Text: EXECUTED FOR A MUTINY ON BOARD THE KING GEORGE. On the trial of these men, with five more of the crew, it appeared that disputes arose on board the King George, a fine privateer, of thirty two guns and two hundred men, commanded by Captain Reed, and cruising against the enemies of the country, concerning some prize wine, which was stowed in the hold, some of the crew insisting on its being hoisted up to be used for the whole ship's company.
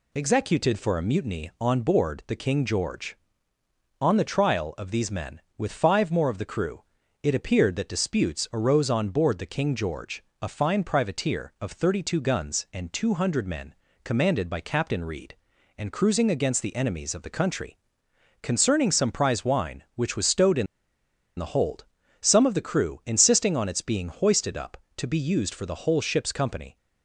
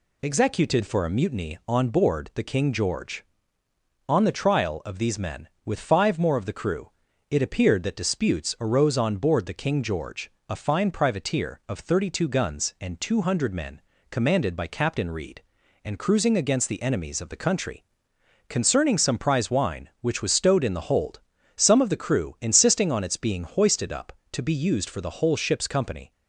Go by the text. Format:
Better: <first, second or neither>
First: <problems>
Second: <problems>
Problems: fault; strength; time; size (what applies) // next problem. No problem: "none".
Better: second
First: pauses between "in" and "the"; noticeable; at 20.6 s; 0.72 s long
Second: none